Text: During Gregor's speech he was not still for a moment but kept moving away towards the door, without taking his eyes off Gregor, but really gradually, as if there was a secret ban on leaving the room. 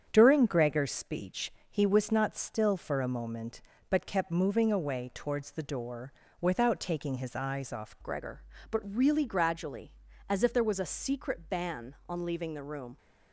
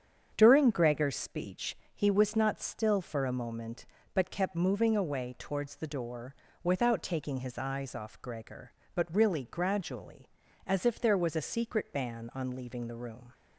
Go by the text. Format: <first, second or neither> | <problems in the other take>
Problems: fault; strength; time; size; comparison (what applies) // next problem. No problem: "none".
second | starts louder than the rest; strong; until 1.1 s; 8 dB; strong in the second // pauses between "speech" and "he"; slight; at 1.5 s; 0.18 s long; slight in the second // changes voice at "Gregor"; from 8.0 s on; 4.9 s long